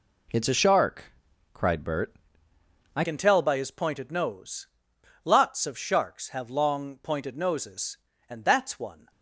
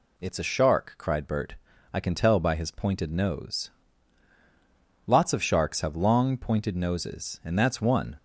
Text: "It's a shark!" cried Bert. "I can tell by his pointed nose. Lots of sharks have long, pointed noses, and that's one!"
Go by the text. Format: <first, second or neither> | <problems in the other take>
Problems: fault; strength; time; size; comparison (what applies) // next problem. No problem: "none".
second | changes voice at "can"; from 3.0 s on; 6.1 s long